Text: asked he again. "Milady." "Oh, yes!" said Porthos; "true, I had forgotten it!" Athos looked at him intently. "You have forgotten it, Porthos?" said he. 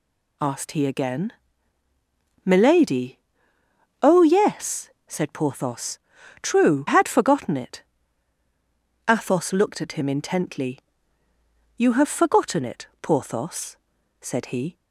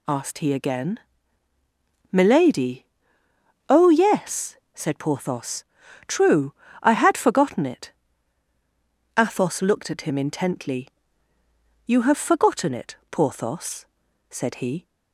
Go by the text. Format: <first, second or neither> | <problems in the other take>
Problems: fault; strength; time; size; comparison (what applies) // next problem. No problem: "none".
second | skips "I"; at 6.8 s